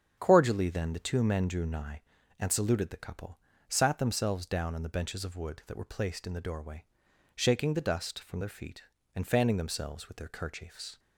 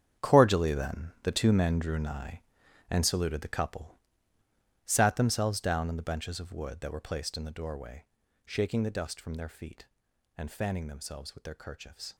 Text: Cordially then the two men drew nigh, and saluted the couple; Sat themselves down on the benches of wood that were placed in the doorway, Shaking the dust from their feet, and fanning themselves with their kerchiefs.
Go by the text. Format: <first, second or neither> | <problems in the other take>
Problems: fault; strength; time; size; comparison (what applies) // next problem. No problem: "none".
first | gets quieter; strong; throughout; 13 dB // starts louder than the rest; strong; until 1.2 s; 8.5 dB; strong in the first